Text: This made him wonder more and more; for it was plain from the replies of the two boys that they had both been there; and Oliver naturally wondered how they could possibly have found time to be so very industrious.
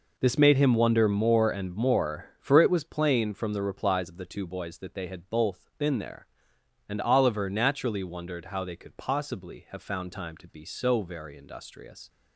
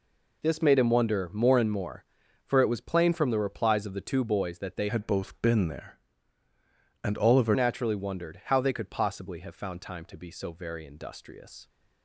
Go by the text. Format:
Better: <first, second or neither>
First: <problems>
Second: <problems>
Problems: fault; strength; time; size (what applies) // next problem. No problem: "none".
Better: first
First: none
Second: changes voice from "had" to "Oliver"; from 4.8 to 7.5 s; 2.7 s long